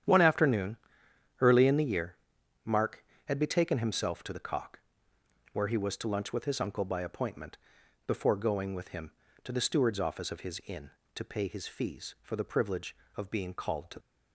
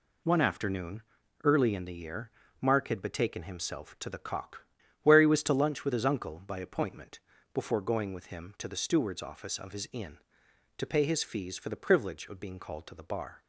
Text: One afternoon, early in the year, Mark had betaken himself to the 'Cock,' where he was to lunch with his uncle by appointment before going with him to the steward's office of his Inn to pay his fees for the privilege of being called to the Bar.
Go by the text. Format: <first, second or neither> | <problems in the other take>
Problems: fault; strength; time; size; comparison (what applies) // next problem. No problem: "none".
second | starts louder than the rest; strong; until 1.7 s; 10 dB // pauses between "appointment" and "before"; noticeable; at 7.5 s; 0.50 s long; slight in the second // stops before "the Bar"; at 14.0 s